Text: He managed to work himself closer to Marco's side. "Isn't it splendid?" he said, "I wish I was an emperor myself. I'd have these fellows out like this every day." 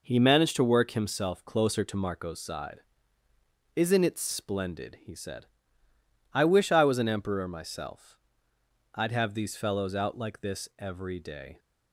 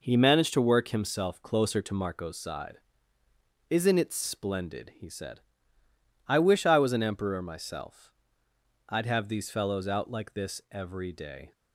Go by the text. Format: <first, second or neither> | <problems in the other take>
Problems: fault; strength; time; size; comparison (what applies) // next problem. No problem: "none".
neither | none